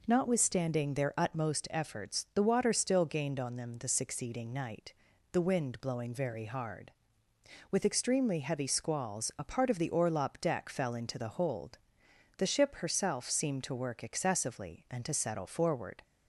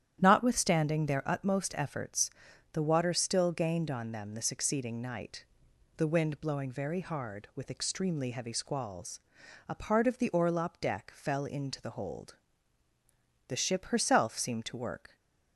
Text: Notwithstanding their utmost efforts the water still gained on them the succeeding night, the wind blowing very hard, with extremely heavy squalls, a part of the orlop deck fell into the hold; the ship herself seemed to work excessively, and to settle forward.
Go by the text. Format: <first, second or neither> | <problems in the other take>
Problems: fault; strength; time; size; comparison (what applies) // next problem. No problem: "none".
first | starts louder than the rest; strong; until 1.2 s; 10.5 dB // pauses between "efforts" and "the"; at 2.2 s; 0.44 s long // stops before "excessively and to settle forward"; at 15.1 s